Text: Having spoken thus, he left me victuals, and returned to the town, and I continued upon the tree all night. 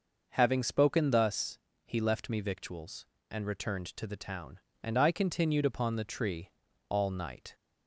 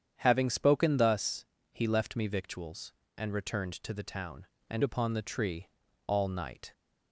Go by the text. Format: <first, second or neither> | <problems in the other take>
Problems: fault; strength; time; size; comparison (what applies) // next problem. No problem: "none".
first | starts louder than the rest; strong; until 1.1 s; 8.5 dB // skips "I continued"; at 4.8 s // pauses between "tree" and "all"; at 5.6 s; 0.38 s long; also in the first